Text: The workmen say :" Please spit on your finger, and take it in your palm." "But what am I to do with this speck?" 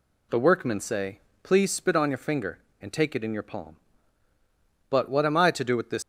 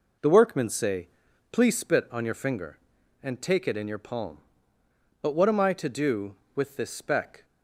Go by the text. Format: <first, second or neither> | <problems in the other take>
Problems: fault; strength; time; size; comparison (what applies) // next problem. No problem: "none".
second | stops before "speck"; at 6.0 s